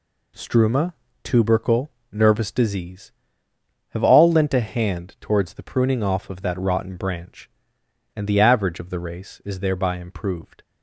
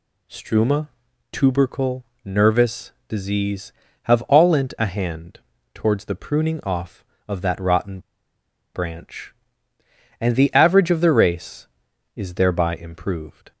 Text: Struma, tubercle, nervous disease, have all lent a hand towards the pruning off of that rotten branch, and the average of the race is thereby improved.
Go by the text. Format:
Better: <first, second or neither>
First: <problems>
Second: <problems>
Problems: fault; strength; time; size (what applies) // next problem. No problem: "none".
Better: first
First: none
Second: pauses between "nervous" and "disease"; slight; at 2.9 s; 0.16 s long // pauses between "hand" and "towards"; slight; at 5.3 s; 0.34 s long // pauses between "rotten" and "branch"; noticeable; at 7.9 s; 0.75 s long